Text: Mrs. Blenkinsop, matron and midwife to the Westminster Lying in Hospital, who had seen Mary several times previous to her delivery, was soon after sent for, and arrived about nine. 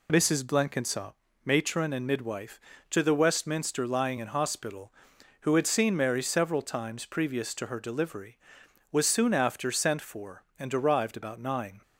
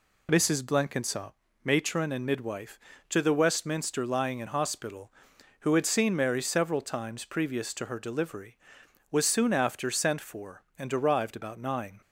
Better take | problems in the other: neither | none

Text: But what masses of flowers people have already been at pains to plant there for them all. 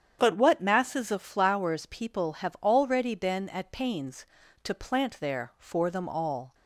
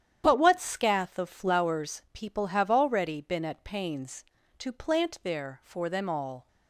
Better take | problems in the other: first | starts louder than the rest; strong; until 1.2 s; 10 dB; strong in the first // says "scath" for "masses"; at 0.5 s

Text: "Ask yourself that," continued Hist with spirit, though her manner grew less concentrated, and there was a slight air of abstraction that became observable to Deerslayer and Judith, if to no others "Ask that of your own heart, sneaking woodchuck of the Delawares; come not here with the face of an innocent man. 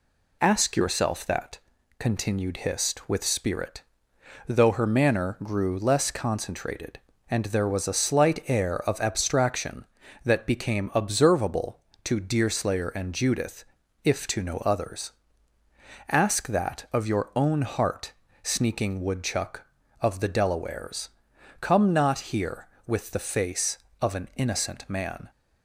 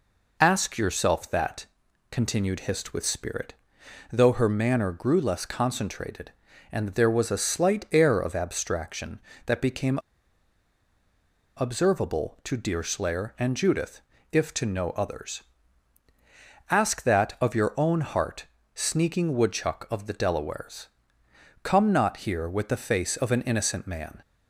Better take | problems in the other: first | pauses between "became" and "observable"; strong; at 9.9 s; 1.5 s long // pauses between "others" and "Ask"; strong; at 15.4 s; 1.2 s long; also in the first

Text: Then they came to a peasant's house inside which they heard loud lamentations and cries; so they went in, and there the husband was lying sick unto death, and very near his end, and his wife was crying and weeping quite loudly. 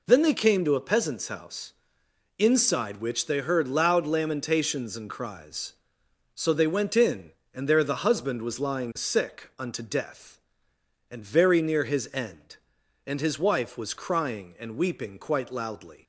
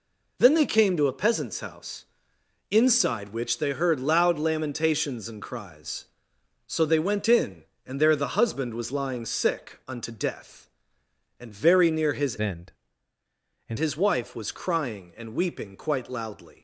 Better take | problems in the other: first | pauses between "house" and "inside"; noticeable; at 2.0 s; 0.66 s long; noticeable in the first // changes voice from "end" to "and"; from 12.4 to 13.7 s; 1.3 s long

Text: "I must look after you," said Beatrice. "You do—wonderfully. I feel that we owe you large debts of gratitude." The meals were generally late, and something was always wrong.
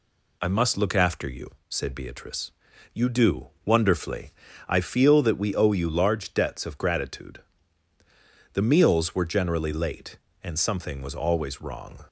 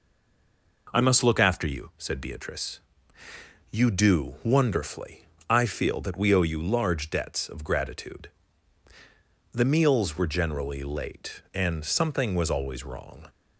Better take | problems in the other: first | stays silent before the first word; slight; until 0.8 s; 0.8 s long

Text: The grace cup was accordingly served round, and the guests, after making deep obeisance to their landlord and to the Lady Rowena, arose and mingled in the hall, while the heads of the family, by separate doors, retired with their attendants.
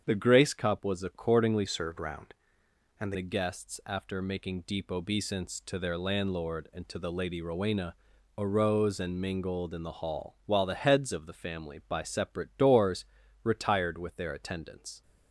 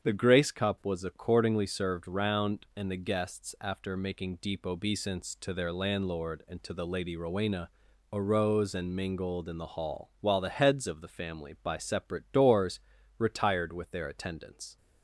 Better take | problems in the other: second | starts louder than the rest; strong; until 1.0 s; 7.5 dB; strong in the second // changes voice from "served" to "and"; from 1.6 to 3.1 s; 1.5 s long

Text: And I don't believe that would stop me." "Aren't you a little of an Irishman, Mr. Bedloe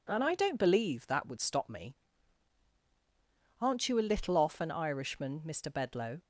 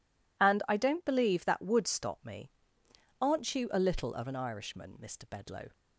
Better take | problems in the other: second | says "off" for "of"; at 4.3 s

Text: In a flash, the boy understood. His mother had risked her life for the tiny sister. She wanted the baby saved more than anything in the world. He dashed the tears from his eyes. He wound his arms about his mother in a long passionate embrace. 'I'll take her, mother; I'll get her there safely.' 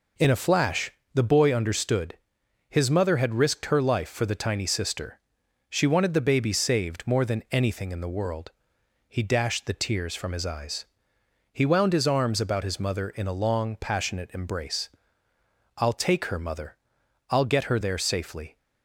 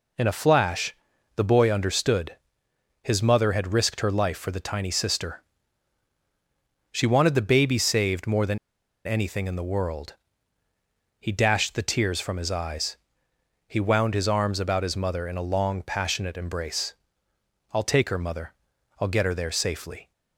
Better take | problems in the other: first | pauses between "than" and "anything"; noticeable; at 8.5 s; 0.49 s long

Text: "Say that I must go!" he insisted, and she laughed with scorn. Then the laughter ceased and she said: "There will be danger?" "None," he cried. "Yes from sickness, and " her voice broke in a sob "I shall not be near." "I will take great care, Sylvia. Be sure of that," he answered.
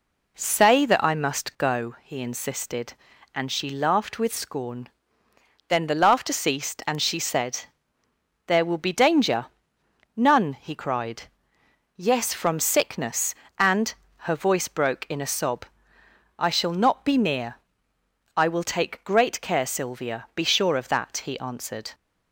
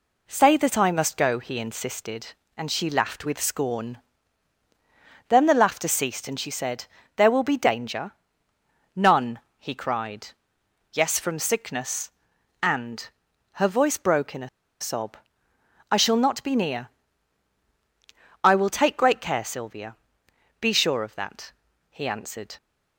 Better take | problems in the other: first | pauses between "a" and "sob"; slight; at 14.4 s; 0.31 s long // pauses between "sob" and "I"; noticeable; at 15.1 s; 0.78 s long; noticeable in the first

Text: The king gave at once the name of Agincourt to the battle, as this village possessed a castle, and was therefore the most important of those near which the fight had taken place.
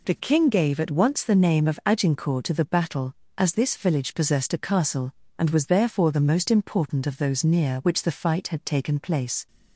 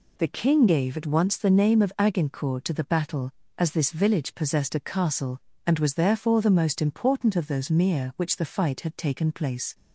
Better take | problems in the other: first | says "mere" for "near"; at 7.7 s

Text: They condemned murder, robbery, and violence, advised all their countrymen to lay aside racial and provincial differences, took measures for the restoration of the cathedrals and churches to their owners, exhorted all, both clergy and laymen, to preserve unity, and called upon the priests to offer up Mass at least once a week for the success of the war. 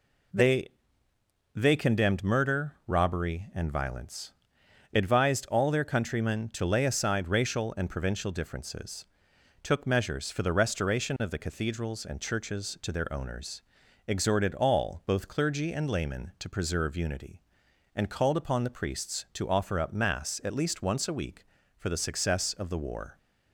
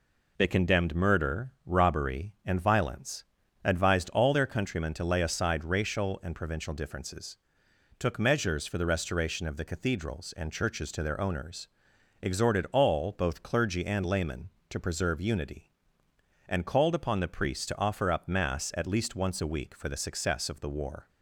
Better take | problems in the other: second | says "They" twice; at 1.5 s

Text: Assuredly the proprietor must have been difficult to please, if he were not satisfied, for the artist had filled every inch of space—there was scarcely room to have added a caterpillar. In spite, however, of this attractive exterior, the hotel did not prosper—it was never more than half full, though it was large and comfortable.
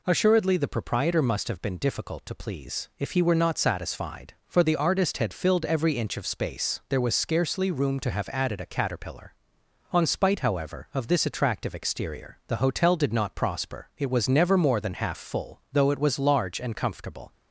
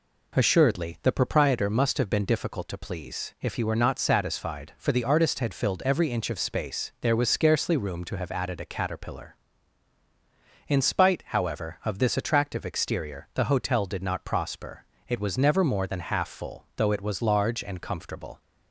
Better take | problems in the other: second | says "On" for "In"; at 9.9 s

